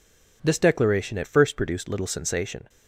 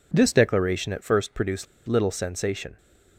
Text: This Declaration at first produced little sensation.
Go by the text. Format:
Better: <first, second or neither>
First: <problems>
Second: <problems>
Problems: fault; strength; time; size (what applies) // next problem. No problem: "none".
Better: first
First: none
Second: pauses between "produced" and "little"; slight; at 1.6 s; 0.21 s long